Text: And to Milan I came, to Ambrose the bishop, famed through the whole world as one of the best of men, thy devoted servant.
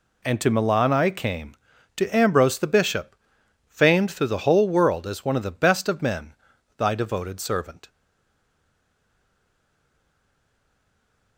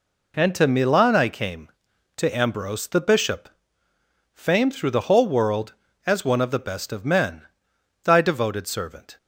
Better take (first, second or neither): second